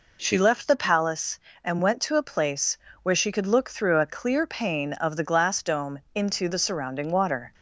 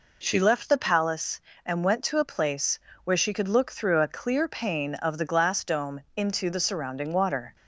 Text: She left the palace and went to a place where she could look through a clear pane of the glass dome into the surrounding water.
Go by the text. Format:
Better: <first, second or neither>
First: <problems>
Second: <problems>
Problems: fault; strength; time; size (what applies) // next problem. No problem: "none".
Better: neither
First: pauses between "place" and "where"; slight; at 2.7 s; 0.28 s long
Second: pauses between "place" and "where"; slight; at 2.7 s; 0.28 s long